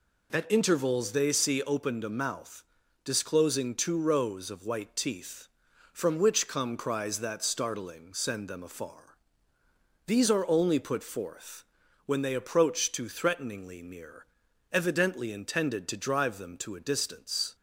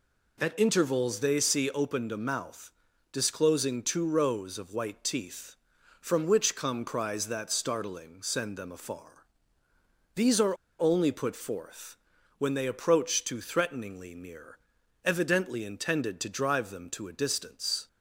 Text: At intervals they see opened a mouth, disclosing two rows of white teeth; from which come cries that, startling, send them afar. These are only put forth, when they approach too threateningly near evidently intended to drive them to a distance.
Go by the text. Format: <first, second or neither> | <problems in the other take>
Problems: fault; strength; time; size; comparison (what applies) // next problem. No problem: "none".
first | pauses between "are" and "only"; slight; at 10.5 s; 0.22 s long // pauses between "near" and "evidently"; at 14.5 s; 0.44 s long; also in the first